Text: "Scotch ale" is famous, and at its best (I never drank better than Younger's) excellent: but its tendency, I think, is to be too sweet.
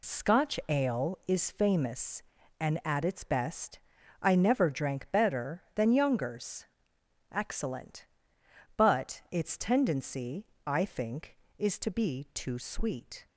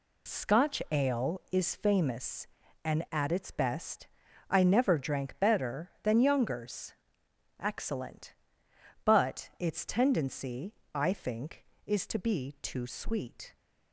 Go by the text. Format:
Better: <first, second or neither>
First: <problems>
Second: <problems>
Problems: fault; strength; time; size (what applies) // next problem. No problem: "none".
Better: neither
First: none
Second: none